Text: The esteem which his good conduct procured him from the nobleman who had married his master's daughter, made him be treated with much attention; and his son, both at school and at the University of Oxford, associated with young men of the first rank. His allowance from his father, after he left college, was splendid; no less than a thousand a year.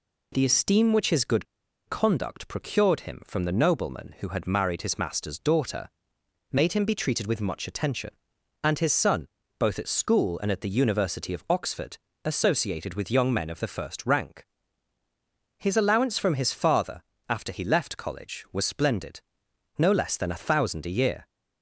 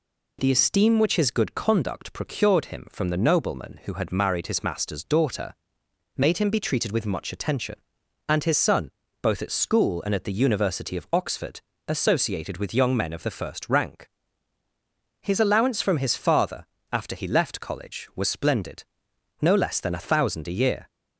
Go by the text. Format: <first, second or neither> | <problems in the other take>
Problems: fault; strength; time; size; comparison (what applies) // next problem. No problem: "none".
second | pauses between "good" and "conduct"; at 1.4 s; 0.43 s long